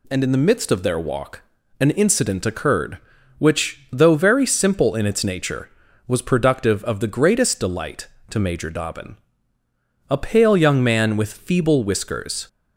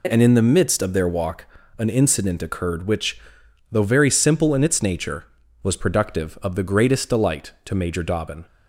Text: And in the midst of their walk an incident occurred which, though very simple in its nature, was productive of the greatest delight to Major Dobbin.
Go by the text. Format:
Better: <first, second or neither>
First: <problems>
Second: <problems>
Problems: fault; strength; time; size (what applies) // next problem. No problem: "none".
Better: second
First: pauses between "walk" and "an"; slight; at 1.4 s; 0.36 s long // goes on to say "A pale young man with feeble whiskers"; strong; from 10.0 s on; 2.3 s long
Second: pauses between "walk" and "an"; slight; at 1.4 s; 0.32 s long